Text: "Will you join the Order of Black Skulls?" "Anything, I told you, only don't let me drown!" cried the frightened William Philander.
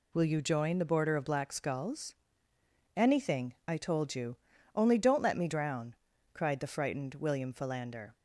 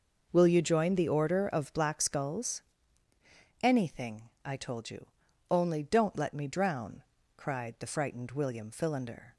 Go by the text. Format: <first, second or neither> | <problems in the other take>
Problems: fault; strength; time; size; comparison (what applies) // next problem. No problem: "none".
second | says "Border" for "Order"; at 0.8 s